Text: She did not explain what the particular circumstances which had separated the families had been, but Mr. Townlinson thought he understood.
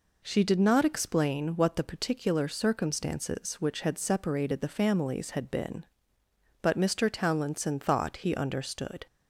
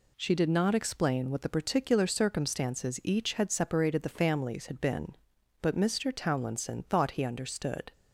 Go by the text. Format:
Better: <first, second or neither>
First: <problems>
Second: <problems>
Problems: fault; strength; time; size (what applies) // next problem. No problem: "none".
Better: first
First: none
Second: says "each" for "which"; at 3.0 s